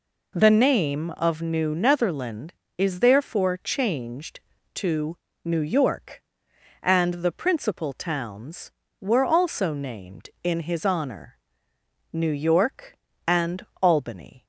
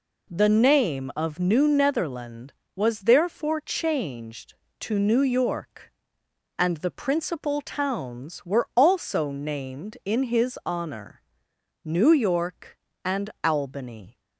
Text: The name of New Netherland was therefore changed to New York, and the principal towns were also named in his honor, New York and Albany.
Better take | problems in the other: second | says "is" for "was"; at 2.7 s // pauses between "to" and "New"; slight; at 5.1 s; 0.28 s long // pauses between "and" and "Albany"; slight; at 13.6 s; 0.16 s long

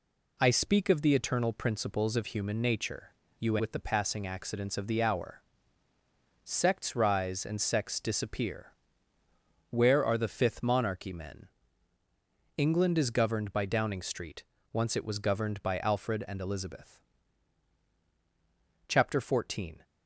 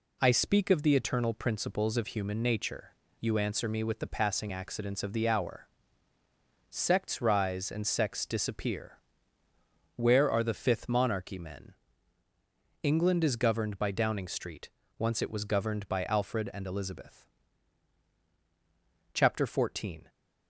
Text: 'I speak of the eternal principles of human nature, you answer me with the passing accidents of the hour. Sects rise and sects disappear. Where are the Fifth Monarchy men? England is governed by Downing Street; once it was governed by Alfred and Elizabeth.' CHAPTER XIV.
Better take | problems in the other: second | skips "answer me"; at 3.5 s

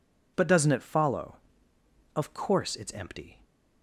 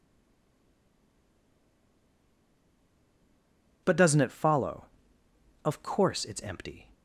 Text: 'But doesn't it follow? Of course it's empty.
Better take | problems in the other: first | stays silent before the first word; strong; until 3.8 s; 3.8 s long

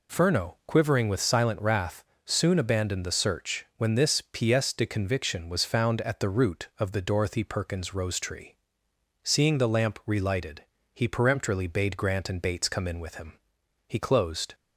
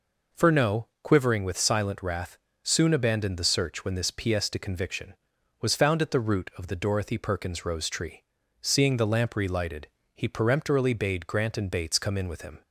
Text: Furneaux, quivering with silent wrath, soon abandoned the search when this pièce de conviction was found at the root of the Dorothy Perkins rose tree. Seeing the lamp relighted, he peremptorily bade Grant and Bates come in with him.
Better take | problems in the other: second | goes on to say "He closed"; noticeable; from 13.8 s on; 0.68 s long

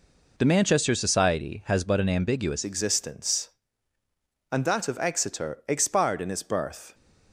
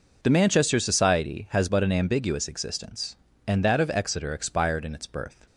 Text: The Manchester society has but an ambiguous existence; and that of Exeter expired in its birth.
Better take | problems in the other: second | changes voice at "existence"; from 2.6 s on; 4.3 s long

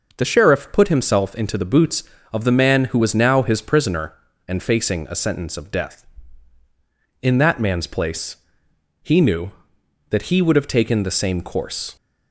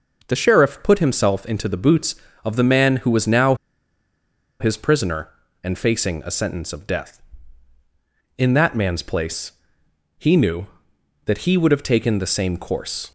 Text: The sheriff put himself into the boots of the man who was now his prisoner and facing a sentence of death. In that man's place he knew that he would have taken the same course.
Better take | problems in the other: first | pauses between "now" and "his"; at 3.5 s; 1.0 s long // pauses between "place" and "he"; noticeable; at 9.5 s; 0.66 s long; noticeable in the first

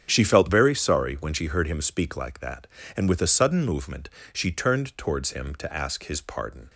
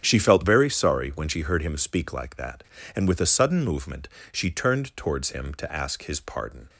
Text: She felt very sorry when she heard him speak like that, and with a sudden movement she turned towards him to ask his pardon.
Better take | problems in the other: neither | starts louder than the rest; strong; the same in both // pauses between "movement" and "she"; slight; the same in both

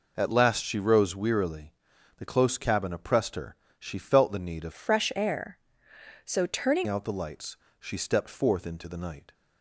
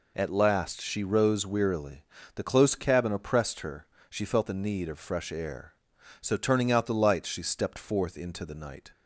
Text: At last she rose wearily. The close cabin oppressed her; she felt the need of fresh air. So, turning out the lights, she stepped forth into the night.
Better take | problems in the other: second | changes voice from "fresh" to "turning"; from 4.7 to 6.8 s; 2.1 s long

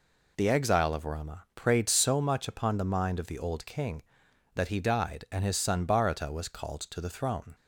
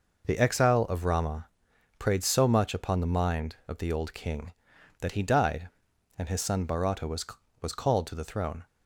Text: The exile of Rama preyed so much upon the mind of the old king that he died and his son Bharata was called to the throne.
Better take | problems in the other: first | pauses between "Rama" and "preyed"; noticeable; at 1.4 s; 0.54 s long // says "was" twice; at 7.6 s

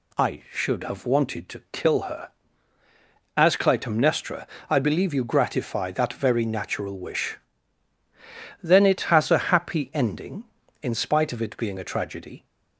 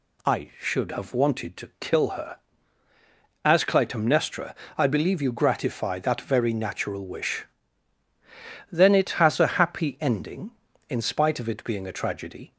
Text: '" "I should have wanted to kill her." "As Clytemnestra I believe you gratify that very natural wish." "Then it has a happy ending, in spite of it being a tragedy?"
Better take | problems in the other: neither | pauses between "Clytemnestra" and "I"; slight; the same in both

